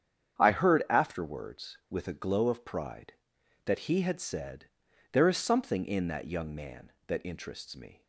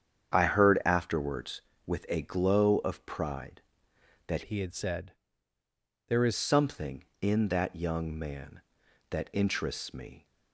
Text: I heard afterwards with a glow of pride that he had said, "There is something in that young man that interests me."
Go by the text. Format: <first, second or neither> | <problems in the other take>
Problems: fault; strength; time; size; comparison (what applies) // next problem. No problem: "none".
first | starts louder than the rest; strong; until 1.3 s; 8 dB; strong in the first // changes voice from "he" to "is"; from 4.4 to 6.3 s; 1.9 s long